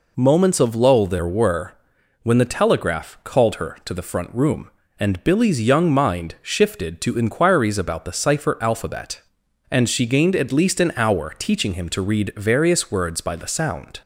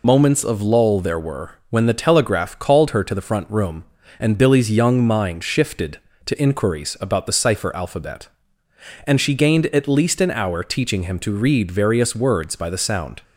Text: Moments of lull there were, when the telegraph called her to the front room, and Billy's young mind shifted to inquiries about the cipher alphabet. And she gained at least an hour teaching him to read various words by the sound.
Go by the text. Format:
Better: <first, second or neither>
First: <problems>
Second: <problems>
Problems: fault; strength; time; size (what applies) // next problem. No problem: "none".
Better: first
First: none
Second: loses the start of "Moments"; at 0.0 s; 45 ms